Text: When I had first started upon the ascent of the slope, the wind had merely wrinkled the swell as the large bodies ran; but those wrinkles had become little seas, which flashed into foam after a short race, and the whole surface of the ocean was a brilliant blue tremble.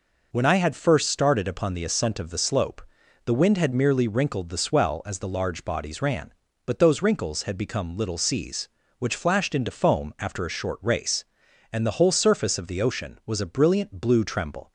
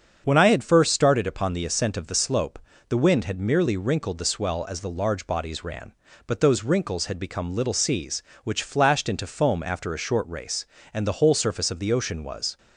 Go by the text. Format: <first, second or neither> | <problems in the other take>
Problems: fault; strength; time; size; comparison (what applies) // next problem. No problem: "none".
first | starts louder than the rest; until 1.2 s; 7 dB // stops before "a brilliant blue tremble"; at 12.5 s